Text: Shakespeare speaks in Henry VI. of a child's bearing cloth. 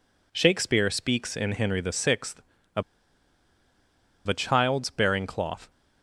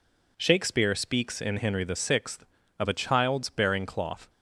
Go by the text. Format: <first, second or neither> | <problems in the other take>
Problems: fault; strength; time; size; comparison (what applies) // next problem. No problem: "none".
second | pauses between "of" and "a"; strong; at 2.8 s; 1.4 s long